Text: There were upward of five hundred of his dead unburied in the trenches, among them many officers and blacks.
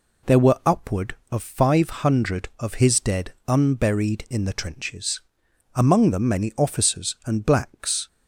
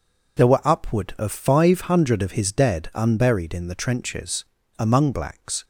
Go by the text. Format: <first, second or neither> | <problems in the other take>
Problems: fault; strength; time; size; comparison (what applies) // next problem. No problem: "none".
first | skips "them many officers and"; at 5.1 s